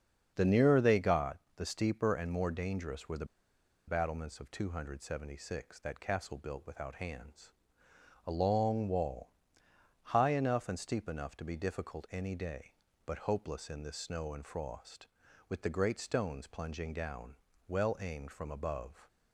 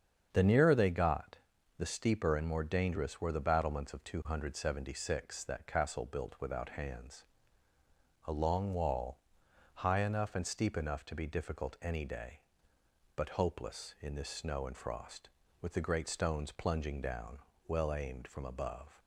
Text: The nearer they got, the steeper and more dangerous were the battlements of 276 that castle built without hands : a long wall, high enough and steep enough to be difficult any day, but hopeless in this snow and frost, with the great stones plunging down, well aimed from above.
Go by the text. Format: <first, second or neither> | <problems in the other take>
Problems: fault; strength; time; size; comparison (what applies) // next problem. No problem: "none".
second | starts louder than the rest; until 1.3 s; 7 dB; strong in the second // pauses between "the" and "battlements"; noticeable; at 3.2 s; 0.62 s long